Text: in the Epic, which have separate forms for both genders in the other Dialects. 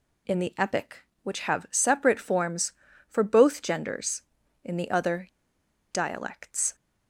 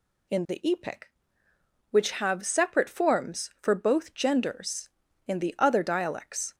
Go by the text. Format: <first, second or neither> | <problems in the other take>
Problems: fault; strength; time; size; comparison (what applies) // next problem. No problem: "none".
second | pauses between "other" and "Dialects"; noticeable; at 5.2 s; 0.64 s long